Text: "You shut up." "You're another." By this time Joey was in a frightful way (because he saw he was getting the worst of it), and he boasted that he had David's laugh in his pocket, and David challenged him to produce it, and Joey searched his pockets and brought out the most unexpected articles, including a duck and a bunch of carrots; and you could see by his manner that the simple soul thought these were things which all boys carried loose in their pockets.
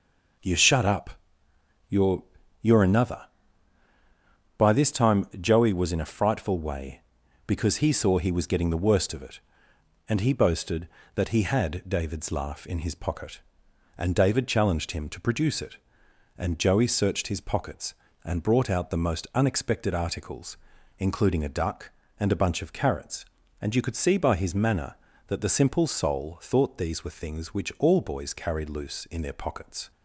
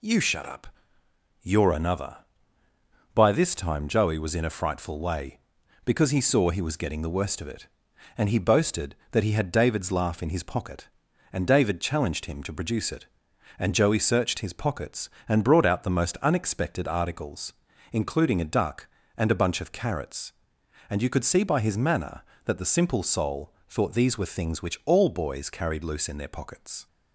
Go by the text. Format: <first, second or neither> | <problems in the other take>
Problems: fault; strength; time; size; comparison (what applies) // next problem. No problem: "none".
second | says "You're" twice; at 2.6 s